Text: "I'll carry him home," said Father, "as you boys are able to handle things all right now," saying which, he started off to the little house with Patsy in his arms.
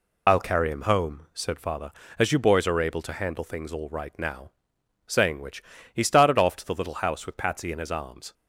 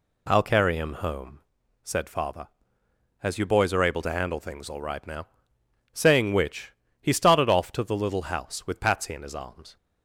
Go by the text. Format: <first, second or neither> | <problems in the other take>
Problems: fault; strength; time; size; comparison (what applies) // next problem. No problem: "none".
second | loses the start of "I'll"; at 0.2 s; 50 ms